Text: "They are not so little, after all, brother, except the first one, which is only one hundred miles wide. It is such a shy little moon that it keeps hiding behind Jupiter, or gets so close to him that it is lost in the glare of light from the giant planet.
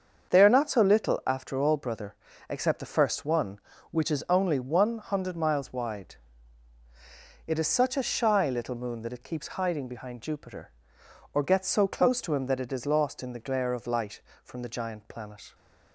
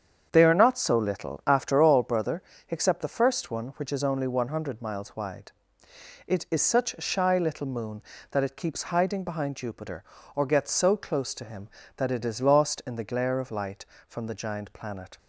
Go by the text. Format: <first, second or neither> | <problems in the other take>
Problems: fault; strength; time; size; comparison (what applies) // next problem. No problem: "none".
neither | starts louder than the rest; the same in both